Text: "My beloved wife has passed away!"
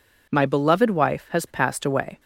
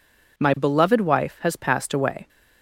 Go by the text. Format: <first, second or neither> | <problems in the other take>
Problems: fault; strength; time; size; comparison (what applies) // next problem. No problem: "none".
neither | none